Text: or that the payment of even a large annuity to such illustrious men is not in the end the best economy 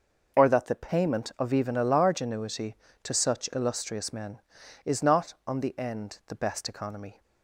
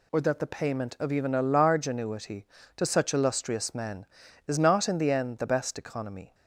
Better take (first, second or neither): second